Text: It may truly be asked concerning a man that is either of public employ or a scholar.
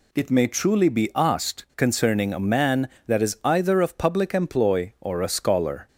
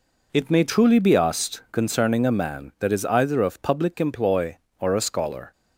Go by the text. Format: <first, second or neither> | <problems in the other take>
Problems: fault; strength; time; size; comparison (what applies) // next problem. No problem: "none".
neither | none